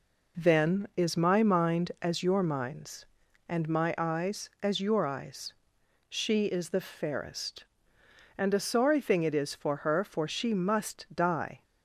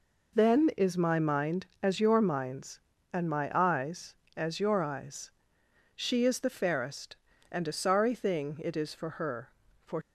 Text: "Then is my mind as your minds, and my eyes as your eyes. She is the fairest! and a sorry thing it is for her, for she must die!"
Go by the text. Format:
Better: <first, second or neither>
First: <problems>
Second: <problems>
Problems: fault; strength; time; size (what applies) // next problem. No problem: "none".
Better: first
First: none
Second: stops before "she must die"; at 10.0 s